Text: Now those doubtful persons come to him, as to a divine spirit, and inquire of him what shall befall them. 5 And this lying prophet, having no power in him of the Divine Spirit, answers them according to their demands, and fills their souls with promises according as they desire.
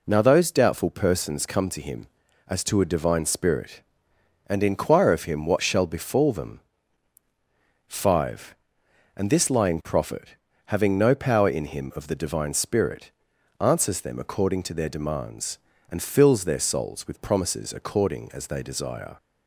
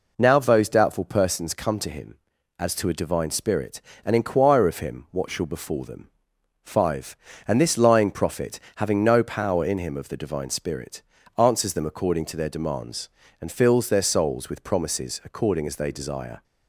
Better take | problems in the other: neither | none

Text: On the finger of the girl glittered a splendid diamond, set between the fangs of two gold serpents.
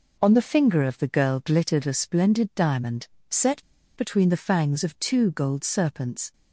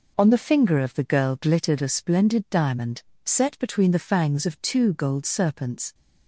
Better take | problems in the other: second | pauses between "set" and "between"; slight; at 3.6 s; 0.34 s long

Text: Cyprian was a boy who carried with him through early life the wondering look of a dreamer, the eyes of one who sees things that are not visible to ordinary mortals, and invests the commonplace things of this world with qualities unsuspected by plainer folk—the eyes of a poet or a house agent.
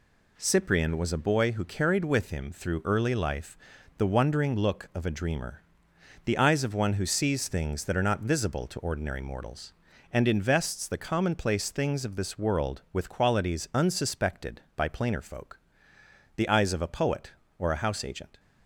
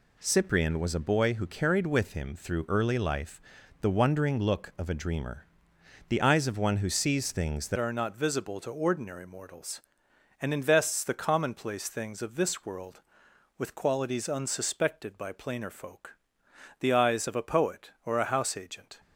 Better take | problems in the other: first | pauses between "life" and "the"; at 3.3 s; 0.42 s long; also in the first // changes voice at "are"; from 7.7 s on; 11.2 s long

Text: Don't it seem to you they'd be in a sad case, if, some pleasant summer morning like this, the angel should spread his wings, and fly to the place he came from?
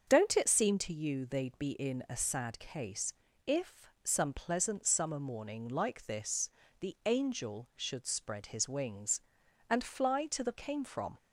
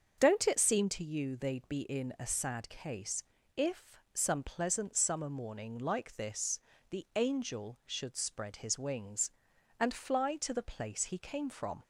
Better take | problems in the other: second | starts louder than the rest; until 1.0 s; 7 dB; also in the second // skips "place he"; at 10.5 s

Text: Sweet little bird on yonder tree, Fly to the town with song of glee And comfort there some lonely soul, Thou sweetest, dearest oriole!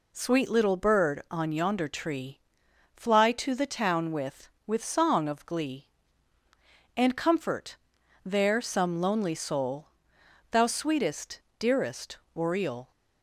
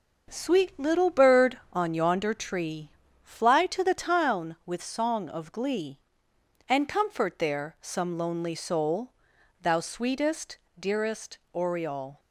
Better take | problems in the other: second | says "with" twice; at 4.6 s // pauses between "comfort" and "there"; noticeable; at 7.7 s; 0.46 s long // pauses between "dearest" and "oriole"; slight; at 12.1 s; 0.16 s long

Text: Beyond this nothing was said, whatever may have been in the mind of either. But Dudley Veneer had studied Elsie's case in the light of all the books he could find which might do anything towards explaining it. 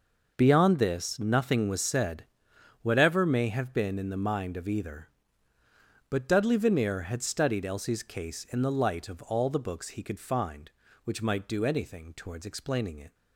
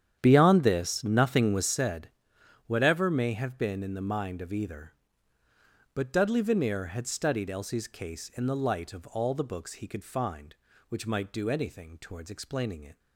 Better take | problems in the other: first | starts louder than the rest; strong; until 1.8 s; 9.5 dB

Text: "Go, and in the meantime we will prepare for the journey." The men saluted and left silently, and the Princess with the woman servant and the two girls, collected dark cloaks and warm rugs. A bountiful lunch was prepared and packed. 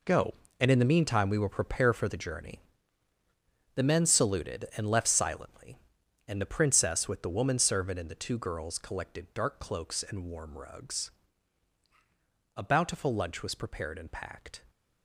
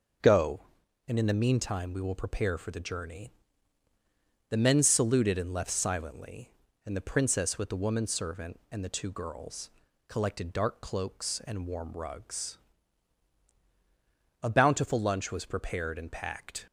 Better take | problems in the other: second | gets quieter; strong; throughout; 11.5 dB

